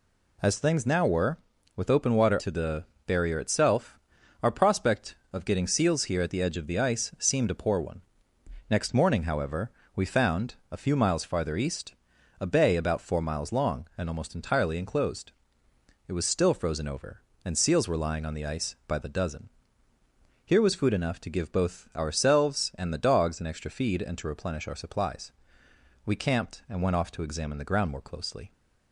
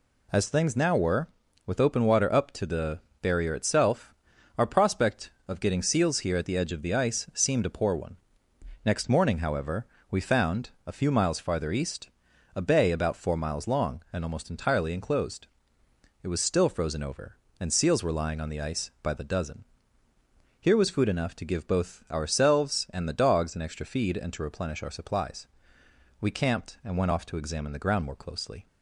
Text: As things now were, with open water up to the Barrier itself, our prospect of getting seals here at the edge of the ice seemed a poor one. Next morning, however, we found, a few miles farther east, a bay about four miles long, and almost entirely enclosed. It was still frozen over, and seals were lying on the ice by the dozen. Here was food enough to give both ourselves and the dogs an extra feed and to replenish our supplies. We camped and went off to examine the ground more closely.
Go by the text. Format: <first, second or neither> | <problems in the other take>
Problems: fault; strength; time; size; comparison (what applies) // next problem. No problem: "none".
second | skips "up"; at 2.3 s // pauses between "the" and "Barrier"; slight; at 2.8 s; 0.22 s long; slight in the second